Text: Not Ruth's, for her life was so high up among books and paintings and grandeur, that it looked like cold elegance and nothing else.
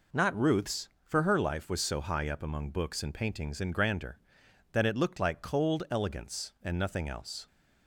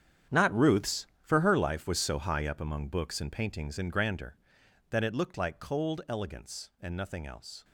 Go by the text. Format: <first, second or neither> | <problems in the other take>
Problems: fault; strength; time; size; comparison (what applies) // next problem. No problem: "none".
first | gets quieter; strong; throughout; 13.5 dB